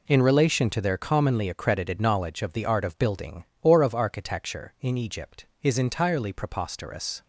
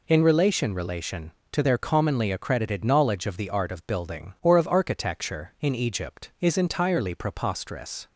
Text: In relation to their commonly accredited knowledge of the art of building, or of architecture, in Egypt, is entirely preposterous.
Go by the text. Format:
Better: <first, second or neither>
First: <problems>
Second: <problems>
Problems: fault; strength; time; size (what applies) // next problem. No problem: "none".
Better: first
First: none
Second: says "relation" twice; at 0.7 s